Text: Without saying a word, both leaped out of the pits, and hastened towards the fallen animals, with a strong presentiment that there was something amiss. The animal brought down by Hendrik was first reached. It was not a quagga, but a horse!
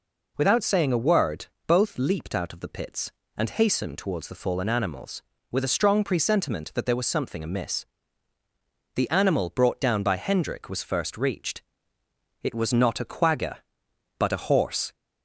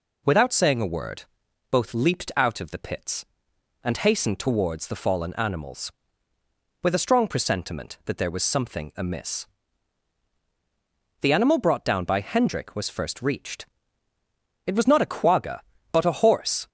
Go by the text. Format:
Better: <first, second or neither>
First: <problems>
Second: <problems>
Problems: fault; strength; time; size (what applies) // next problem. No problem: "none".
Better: neither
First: none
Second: none